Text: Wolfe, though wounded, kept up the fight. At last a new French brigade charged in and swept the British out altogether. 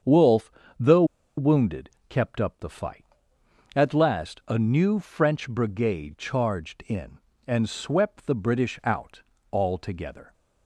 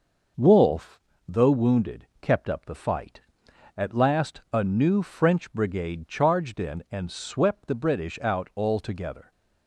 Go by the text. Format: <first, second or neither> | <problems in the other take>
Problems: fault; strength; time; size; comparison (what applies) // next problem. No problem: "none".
second | starts louder than the rest; strong; until 1.6 s; 7.5 dB // pauses between "though" and "wounded"; slight; at 1.0 s; 0.33 s long // pauses between "out" and "altogether"; slight; at 9.2 s; 0.32 s long